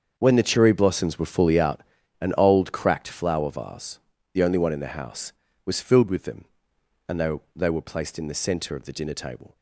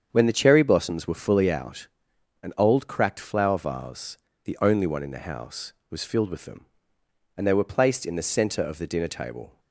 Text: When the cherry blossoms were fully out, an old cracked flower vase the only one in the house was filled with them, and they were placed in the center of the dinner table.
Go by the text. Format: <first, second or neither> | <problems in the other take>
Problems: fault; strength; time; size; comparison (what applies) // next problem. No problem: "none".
second | starts louder than the rest; until 1.1 s; 7 dB; strong in the second // pauses between "vase" and "the"; slight; at 3.9 s; 0.34 s long; slight in the second // says "they" twice; at 7.5 s